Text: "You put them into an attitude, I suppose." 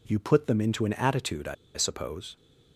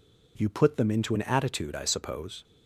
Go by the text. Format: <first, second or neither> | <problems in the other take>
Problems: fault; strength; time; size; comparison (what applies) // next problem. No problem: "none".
second | pauses between "I" and "suppose"; slight; at 1.5 s; 0.20 s long